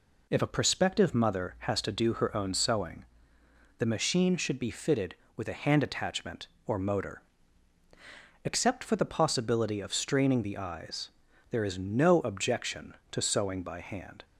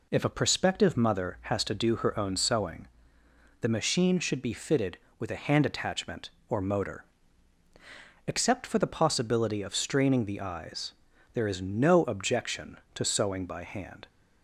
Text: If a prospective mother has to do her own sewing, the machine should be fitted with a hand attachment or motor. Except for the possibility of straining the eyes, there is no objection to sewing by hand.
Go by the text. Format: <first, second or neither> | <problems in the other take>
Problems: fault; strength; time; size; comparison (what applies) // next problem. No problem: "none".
neither | none